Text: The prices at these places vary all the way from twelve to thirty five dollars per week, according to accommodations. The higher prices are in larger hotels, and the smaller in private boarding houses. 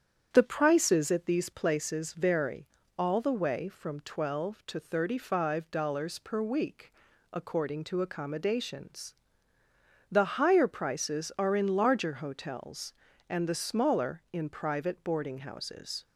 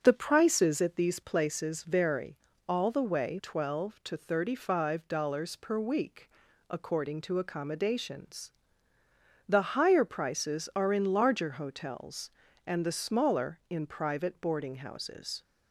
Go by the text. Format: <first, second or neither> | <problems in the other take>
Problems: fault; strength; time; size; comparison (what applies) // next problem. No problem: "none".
first | starts louder than the rest; strong; until 1.0 s; 7.5 dB; strong in the first // pauses between "vary" and "all"; slight; at 2.3 s; 0.28 s long; slight in the first // skips "from"; at 3.3 s